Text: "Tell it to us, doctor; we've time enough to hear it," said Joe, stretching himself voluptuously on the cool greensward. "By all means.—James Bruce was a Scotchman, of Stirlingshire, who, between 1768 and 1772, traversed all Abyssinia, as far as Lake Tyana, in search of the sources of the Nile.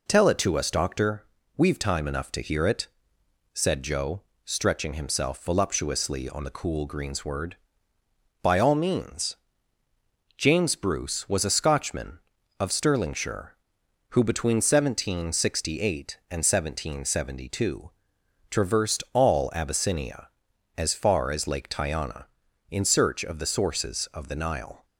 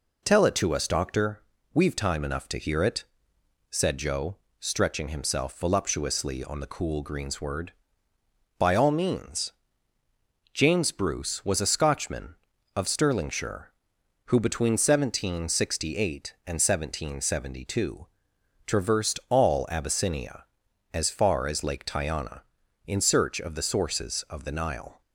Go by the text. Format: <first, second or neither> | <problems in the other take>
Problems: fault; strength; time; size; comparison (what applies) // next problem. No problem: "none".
neither | none